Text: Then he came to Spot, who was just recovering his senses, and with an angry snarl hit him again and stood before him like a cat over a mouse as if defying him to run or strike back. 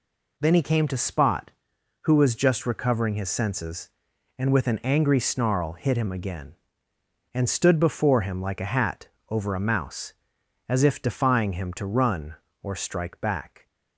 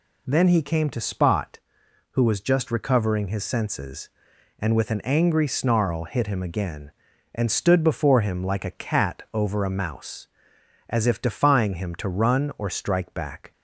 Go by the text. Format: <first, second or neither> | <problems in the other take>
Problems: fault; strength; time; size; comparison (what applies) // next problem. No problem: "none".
second | says "hat" for "cat"; at 8.6 s